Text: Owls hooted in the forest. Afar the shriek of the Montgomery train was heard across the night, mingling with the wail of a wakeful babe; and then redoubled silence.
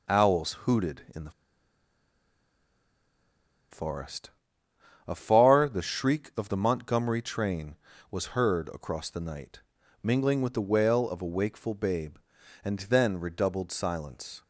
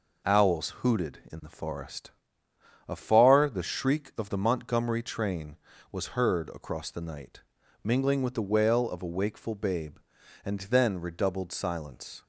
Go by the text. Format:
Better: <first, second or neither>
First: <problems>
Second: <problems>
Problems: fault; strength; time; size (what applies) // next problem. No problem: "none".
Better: second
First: pauses between "the" and "forest"; strong; at 1.2 s; 2.4 s long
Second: none